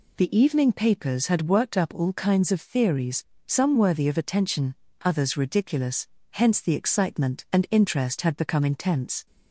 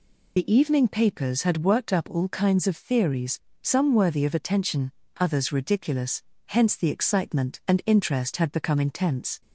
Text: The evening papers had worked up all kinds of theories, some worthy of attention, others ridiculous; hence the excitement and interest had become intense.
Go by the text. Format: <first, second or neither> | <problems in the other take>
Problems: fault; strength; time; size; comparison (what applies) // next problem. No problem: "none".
first | loses the start of "The"; at 0.3 s; 40 ms